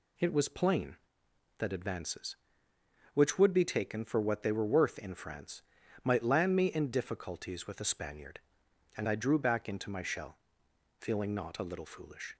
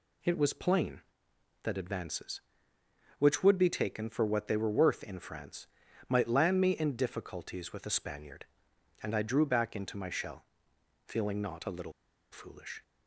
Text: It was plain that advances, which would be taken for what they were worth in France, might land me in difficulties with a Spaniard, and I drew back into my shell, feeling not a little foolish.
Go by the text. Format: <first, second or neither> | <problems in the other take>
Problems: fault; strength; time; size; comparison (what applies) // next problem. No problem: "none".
first | pauses between "little" and "foolish"; at 11.9 s; 0.39 s long